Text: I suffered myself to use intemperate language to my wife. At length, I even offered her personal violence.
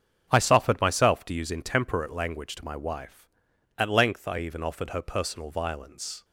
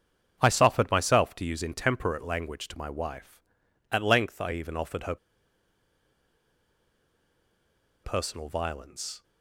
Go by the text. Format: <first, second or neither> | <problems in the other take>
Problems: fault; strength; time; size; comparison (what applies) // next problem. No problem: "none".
first | starts louder than the rest; strong; until 1.4 s; 7 dB; strong in the first // pauses between "her" and "personal"; strong; at 5.1 s; 2.8 s long